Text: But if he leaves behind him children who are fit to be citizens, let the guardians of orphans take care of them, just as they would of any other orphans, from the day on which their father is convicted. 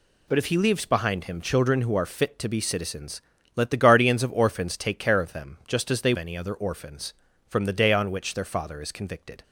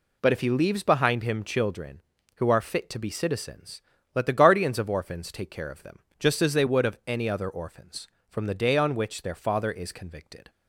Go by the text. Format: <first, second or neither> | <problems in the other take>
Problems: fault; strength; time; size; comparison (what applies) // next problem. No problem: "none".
second | skips "would of"; at 6.1 s